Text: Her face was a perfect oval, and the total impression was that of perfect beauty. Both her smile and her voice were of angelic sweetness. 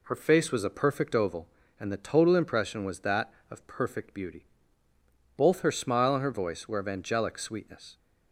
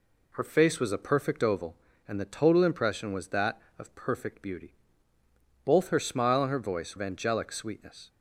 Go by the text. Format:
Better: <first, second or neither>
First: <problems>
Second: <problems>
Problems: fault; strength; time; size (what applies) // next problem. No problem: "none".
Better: first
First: none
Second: skips "were"; at 6.9 s